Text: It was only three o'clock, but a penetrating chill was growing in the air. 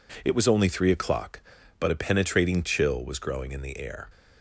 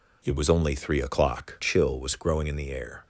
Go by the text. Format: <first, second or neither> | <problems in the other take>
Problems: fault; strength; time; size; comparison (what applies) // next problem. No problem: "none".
first | skips "but a penetrating"; at 1.5 s